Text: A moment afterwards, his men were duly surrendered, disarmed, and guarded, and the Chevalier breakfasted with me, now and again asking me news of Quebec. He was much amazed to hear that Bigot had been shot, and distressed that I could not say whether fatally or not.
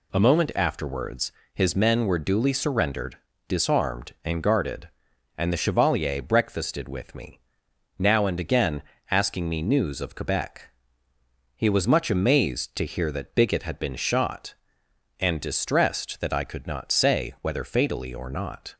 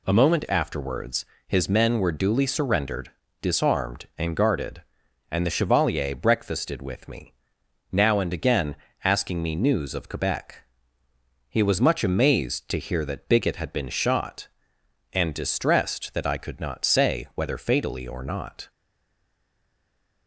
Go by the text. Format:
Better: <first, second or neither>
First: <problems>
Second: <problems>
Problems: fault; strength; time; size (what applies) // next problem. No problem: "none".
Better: first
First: pauses between "again" and "asking"; slight; at 8.8 s; 0.28 s long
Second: pauses between "again" and "asking"; slight; at 8.7 s; 0.28 s long // stays silent after the last word; noticeable; from 18.7 s on; 1.5 s long